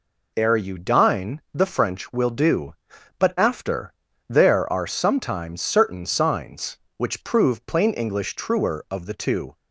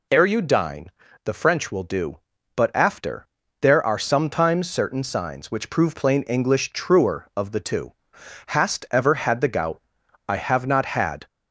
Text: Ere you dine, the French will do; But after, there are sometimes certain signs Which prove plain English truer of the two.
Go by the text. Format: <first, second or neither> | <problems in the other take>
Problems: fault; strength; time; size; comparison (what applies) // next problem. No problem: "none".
first | goes on to say "Hast ever had the gout I have not had"; strong; from 8.4 s on; 2.8 s long